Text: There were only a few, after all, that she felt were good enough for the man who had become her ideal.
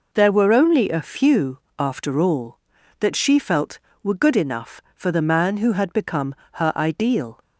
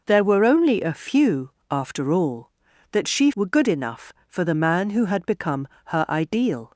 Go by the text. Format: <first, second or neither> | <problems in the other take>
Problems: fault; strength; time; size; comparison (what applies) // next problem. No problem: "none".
first | skips "felt"; at 3.3 s // pauses between "become" and "her"; slight; at 5.6 s; 0.20 s long; slight in the first